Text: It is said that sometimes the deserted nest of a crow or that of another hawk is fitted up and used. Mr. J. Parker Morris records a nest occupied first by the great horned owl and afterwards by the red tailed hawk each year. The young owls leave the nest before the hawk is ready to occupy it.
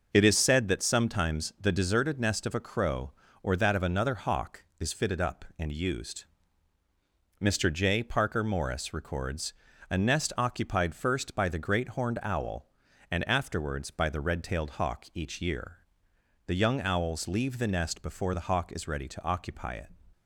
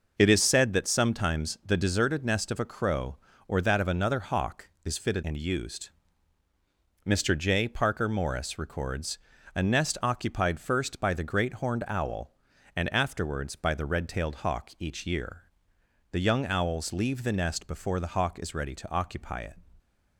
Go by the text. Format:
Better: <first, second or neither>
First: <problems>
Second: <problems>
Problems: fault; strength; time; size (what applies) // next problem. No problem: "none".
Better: first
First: pauses between "records" and "a"; slight; at 9.5 s; 0.36 s long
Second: skips "up"; at 5.2 s // pauses between "records" and "a"; slight; at 9.1 s; 0.36 s long